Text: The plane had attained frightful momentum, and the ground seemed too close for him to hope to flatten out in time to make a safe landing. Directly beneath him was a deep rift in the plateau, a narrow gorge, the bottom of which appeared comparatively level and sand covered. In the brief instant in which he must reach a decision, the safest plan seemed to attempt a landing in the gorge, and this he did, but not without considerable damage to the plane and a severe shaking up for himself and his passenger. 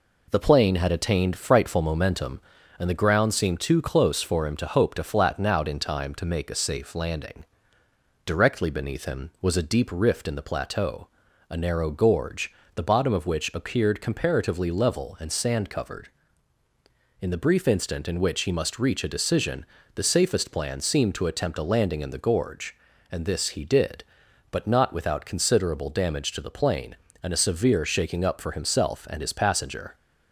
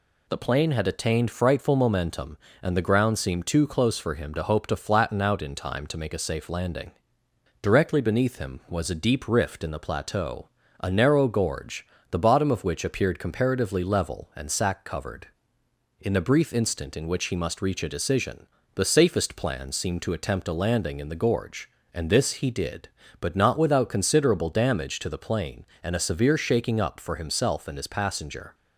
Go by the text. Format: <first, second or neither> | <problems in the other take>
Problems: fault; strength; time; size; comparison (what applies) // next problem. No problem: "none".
first | says "sack" for "sand"; at 14.5 s